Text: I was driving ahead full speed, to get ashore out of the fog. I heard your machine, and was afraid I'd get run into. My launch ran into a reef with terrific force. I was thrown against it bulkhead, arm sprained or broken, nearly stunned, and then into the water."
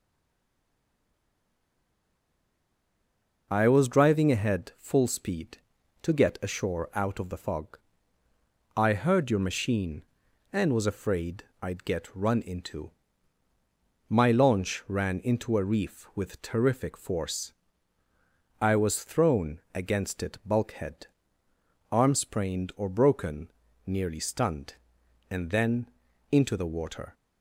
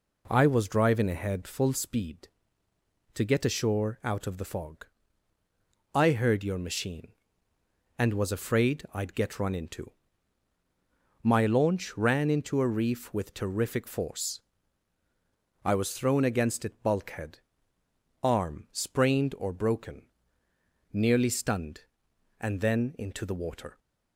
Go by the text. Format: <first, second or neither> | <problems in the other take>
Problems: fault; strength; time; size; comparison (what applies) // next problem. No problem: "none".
second | stays silent before the first word; strong; until 3.4 s; 3.4 s long // pauses between "afraid" and "I'd"; slight; at 11.4 s; 0.18 s long // pauses between "then" and "into"; noticeable; at 25.8 s; 0.46 s long